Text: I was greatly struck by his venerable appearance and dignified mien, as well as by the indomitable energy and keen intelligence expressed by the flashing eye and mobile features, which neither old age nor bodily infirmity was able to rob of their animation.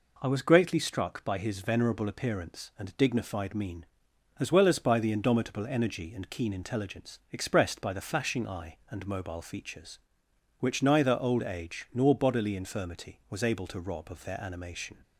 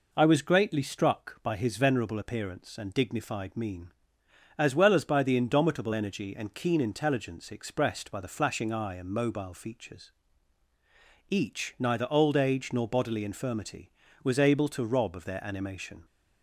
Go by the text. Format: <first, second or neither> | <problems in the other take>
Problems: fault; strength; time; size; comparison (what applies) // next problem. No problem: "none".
first | says "each" for "which"; at 11.2 s